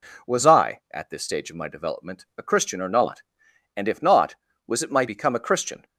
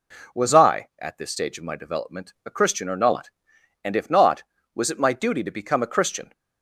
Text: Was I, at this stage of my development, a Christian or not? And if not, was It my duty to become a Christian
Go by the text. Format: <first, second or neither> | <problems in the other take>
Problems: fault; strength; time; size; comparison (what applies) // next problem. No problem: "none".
second | skips "duty to"; at 5.0 s